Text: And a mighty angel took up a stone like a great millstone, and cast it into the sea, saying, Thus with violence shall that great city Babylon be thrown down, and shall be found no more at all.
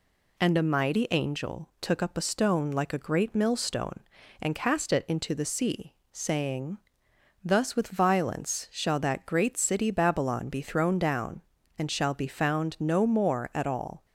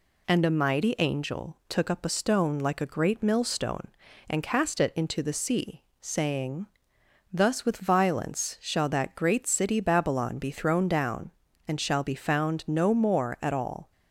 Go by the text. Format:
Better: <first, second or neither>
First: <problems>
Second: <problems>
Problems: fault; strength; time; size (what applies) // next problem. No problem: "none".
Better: neither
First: none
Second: none